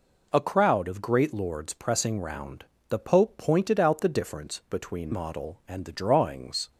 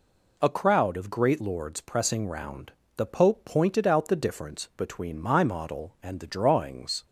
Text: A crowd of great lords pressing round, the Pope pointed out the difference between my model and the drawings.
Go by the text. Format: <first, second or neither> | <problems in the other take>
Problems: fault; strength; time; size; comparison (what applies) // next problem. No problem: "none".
second | skips "my"; at 5.1 s